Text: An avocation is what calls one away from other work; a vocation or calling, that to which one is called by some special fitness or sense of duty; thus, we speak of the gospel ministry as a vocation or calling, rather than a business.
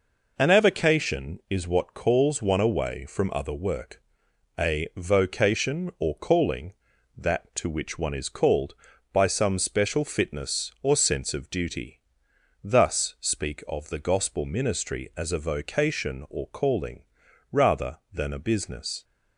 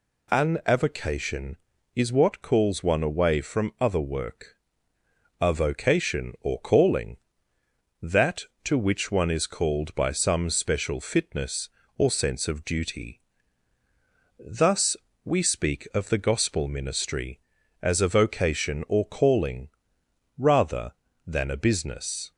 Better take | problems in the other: second | skips "we"; at 13.1 s

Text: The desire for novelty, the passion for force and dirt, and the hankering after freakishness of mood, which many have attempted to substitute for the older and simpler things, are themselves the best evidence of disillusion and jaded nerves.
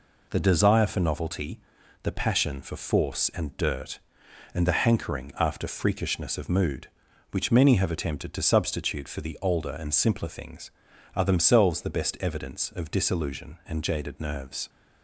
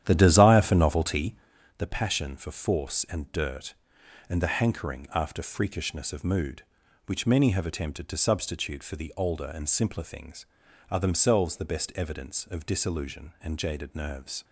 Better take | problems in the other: first | starts louder than the rest; strong; until 1.6 s; 10.5 dB

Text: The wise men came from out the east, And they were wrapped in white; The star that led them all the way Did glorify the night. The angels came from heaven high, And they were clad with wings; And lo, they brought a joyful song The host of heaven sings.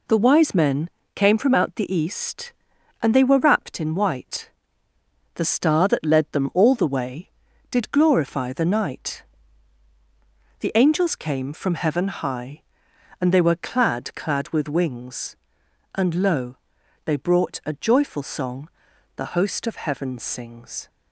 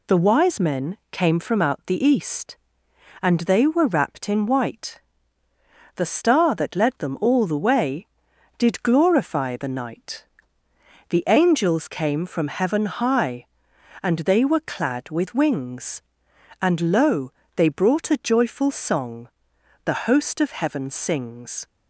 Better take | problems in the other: second | pauses between "men" and "came"; slight; at 0.8 s; 0.28 s long; slight in the second // says "clad" twice; at 14.1 s // pauses between "song" and "The"; noticeable; at 18.6 s; 0.48 s long; noticeable in the second

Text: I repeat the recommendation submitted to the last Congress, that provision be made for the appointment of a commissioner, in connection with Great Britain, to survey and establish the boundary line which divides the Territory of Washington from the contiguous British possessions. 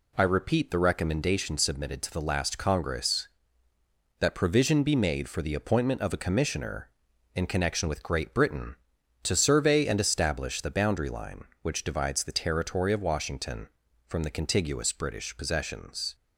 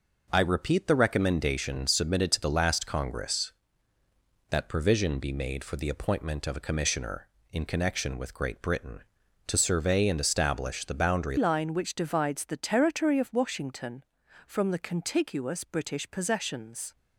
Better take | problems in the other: first | changes voice at "line"; from 11.3 s on; 5.6 s long

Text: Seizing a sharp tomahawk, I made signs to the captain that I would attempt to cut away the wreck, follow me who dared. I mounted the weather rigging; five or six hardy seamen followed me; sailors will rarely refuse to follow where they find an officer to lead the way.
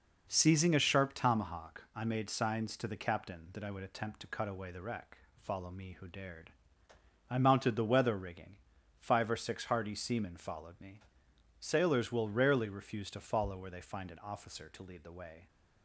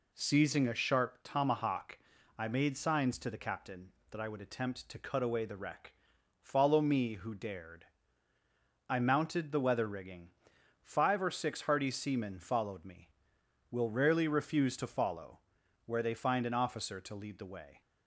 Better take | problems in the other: first | skips "sailors"; at 13.3 s // pauses between "follow" and "where"; noticeable; at 15.3 s; 0.48 s long

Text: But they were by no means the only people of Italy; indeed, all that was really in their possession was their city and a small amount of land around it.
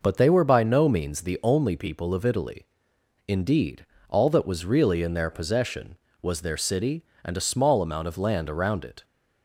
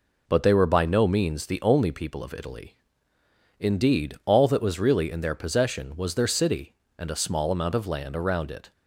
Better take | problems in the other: neither | none

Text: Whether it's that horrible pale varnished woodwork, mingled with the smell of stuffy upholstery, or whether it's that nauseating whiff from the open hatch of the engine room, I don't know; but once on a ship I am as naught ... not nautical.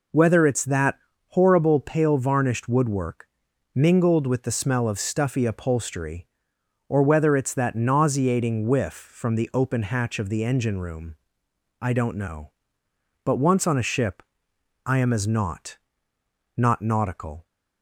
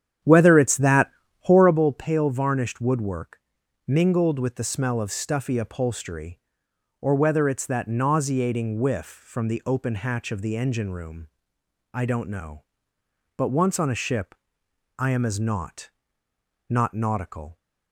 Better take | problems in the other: first | starts louder than the rest; strong; until 1.9 s; 9.5 dB // pauses between "that" and "horrible"; slight; at 1.1 s; 0.30 s long; slight in the first // pauses between "ship" and "I"; noticeable; at 14.3 s; 0.60 s long; noticeable in the first

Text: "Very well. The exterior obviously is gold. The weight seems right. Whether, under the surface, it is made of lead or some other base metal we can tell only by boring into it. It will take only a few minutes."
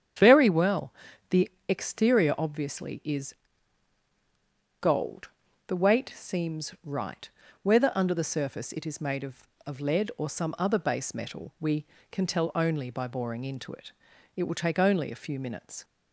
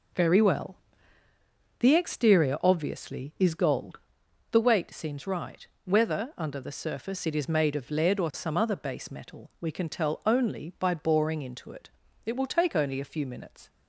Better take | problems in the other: second | starts louder than the rest; strong; until 1.7 s; 8.5 dB // pauses between "The" and "exterior"; slight; at 1.4 s; 0.20 s long // pauses between "is" and "gold"; strong; at 3.3 s; 1.4 s long // says "of" twice; at 9.6 s

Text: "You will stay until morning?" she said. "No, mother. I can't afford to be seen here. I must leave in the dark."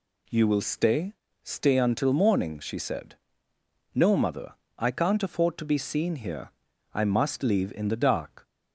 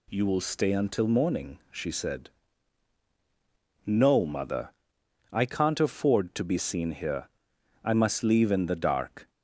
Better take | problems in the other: second | says "stay" twice; at 1.4 s

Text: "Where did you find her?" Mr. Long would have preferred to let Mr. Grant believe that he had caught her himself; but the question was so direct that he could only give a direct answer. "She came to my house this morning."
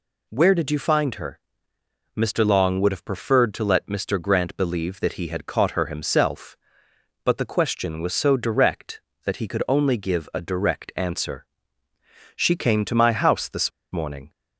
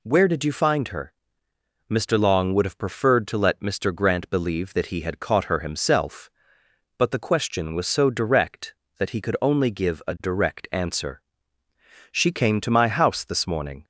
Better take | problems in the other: second | pauses between "this" and "morning"; slight; at 13.6 s; 0.23 s long

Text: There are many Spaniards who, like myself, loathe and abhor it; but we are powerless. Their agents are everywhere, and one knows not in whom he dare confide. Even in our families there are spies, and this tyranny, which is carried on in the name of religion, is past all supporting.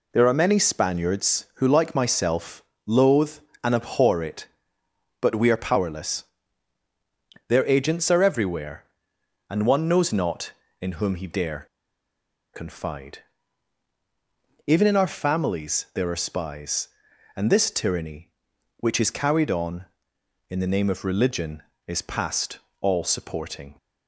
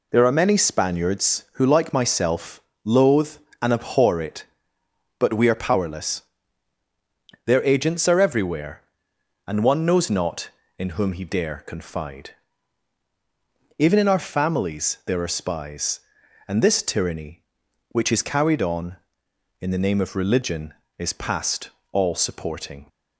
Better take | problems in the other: second | pauses between "dare" and "confide"; noticeable; at 11.6 s; 0.89 s long // pauses between "past" and "all"; slight; at 22.5 s; 0.22 s long; slight in the second

